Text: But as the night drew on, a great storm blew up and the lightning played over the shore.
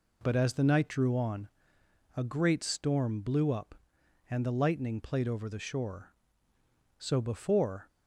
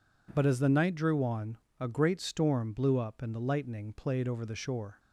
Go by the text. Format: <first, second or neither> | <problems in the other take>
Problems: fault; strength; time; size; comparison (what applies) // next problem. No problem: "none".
second | goes on to say "So before"; noticeable; from 6.9 s on; 0.90 s long